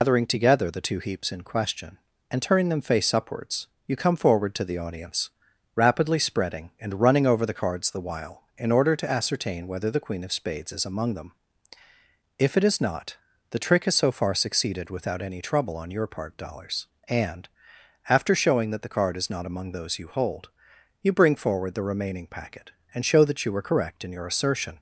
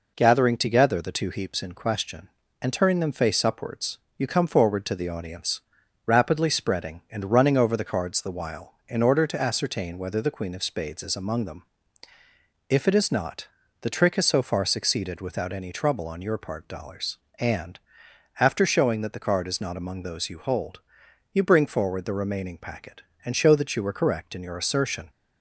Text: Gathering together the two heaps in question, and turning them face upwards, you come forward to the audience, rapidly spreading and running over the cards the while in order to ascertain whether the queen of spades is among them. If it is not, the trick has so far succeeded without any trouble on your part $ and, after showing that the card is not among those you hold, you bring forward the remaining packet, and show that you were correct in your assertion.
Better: second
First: loses the start of "Gathering"; at 0.0 s; 160 ms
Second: none

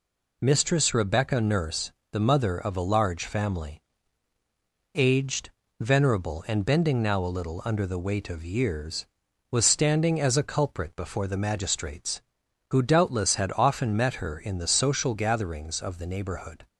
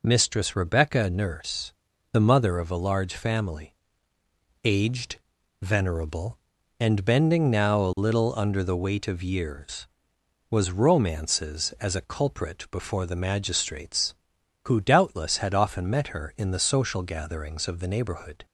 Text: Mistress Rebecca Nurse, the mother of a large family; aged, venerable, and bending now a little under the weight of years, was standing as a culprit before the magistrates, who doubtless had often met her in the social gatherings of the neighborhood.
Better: first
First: none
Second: says "romances" for "standing"; at 10.7 s

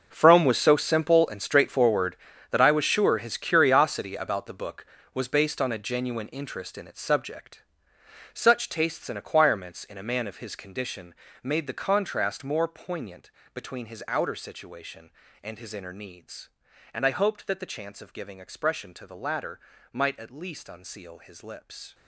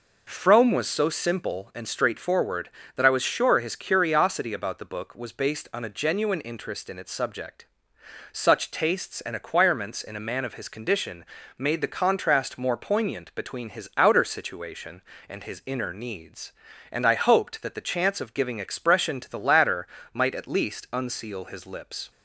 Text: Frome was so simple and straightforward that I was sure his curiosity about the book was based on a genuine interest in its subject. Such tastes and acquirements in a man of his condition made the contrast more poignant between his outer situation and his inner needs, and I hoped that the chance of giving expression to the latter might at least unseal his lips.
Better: second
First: gets quieter; strong; throughout; 15 dB // pauses between "condition" and "made"; slight; at 11.1 s; 0.28 s long // pauses between "poignant" and "between"; slight; at 13.3 s; 0.24 s long // pauses between "latter" and "might"; slight; at 19.5 s; 0.34 s long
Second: pauses between "condition" and "made"; slight; at 11.2 s; 0.34 s long // pauses between "latter" and "might"; slight; at 19.8 s; 0.24 s long

